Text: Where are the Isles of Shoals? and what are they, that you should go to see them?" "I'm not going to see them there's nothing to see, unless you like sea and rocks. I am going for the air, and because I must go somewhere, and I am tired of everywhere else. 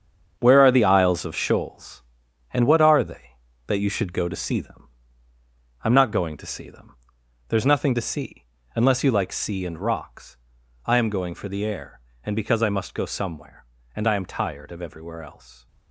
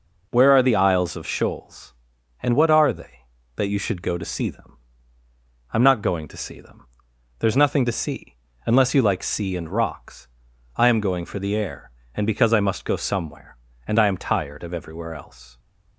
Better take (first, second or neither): second